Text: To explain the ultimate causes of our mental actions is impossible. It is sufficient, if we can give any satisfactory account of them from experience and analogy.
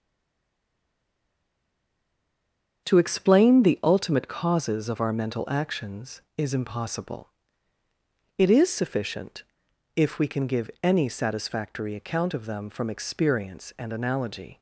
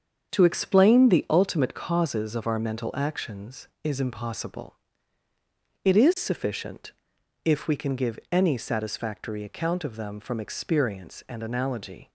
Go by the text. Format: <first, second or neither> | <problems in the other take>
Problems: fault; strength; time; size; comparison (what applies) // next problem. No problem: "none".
second | stays silent before the first word; strong; until 2.8 s; 2.8 s long // starts louder than the rest; strong; until 3.8 s; 7.5 dB; strong in the second